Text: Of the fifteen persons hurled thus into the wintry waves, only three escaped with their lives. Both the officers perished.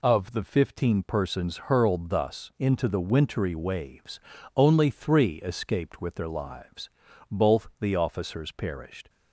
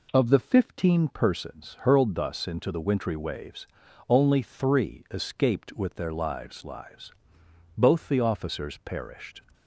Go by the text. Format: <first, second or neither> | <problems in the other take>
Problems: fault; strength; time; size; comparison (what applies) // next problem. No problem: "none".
first | says "lives" twice; at 6.6 s